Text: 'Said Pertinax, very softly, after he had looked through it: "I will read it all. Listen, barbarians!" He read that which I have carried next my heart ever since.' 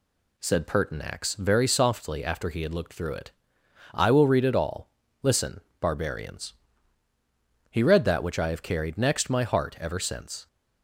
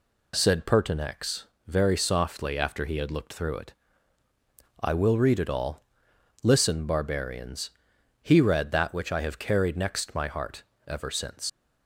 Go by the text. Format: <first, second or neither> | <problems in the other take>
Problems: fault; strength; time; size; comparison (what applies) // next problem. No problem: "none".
first | pauses between "heart" and "ever"; slight; at 10.6 s; 0.24 s long // leaves "since" unfinished; at 11.4 s; 45 ms